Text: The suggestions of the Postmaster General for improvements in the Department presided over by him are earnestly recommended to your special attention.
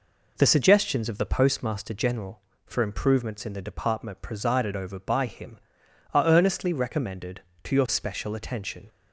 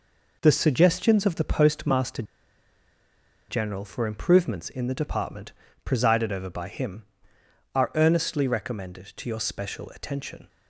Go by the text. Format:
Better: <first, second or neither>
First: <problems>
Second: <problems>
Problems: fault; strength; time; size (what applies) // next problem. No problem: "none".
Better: first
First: none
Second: pauses between "Postmaster" and "General"; strong; at 2.2 s; 1.2 s long // pauses between "Department" and "presided"; slight; at 5.5 s; 0.32 s long